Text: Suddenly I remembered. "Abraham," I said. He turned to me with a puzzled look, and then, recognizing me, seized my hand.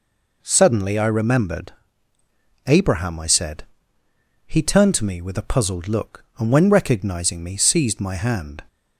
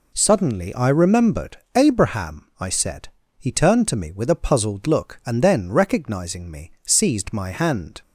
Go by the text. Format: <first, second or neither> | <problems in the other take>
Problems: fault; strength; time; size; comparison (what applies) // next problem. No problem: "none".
second | says "when" for "then"; at 6.4 s